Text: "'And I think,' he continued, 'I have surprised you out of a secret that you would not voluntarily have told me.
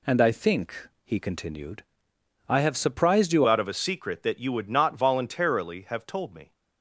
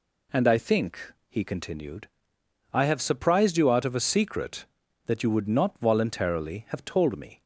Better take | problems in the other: second | changes voice at "out"; from 3.4 s on; 3.1 s long

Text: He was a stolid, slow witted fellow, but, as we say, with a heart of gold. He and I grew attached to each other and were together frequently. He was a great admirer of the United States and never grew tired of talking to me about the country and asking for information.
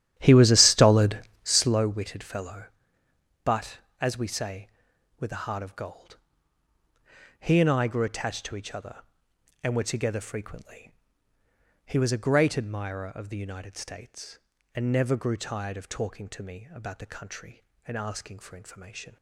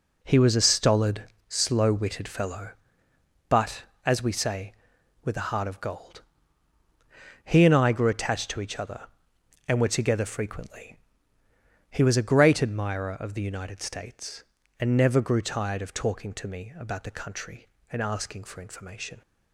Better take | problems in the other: second | starts louder than the rest; strong; until 1.9 s; 11.5 dB

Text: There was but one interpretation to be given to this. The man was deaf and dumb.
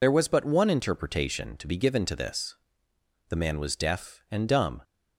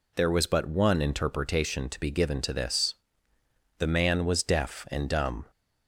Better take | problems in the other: second | loses the start of "There"; at 0.0 s; 50 ms

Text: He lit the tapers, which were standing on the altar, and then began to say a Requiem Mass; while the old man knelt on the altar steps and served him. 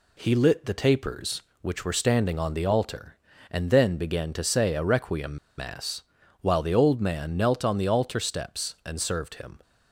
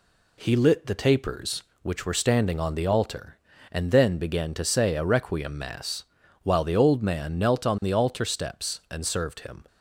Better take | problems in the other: second | pauses between "Requiem" and "Mass"; slight; at 5.3 s; 0.19 s long

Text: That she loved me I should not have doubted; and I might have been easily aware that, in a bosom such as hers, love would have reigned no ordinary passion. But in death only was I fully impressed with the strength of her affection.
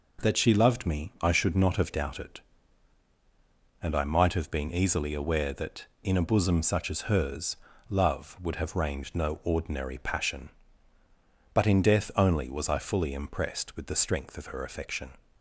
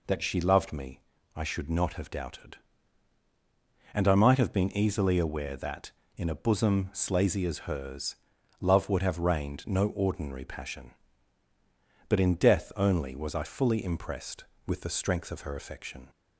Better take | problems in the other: first | pauses between "me" and "I"; slight; at 1.0 s; 0.34 s long // says "slazy" for "such"; at 6.9 s

